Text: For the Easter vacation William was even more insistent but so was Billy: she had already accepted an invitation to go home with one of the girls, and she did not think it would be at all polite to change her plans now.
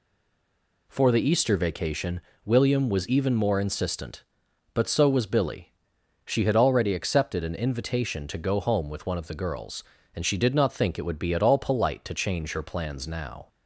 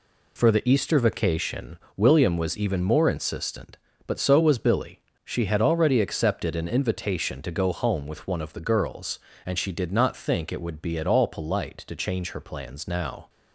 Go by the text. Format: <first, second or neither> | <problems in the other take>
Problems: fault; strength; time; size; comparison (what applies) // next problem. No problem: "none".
second | stays silent before the first word; slight; until 0.8 s; 0.8 s long // pauses between "vacation" and "William"; slight; at 2.2 s; 0.24 s long; slight in the second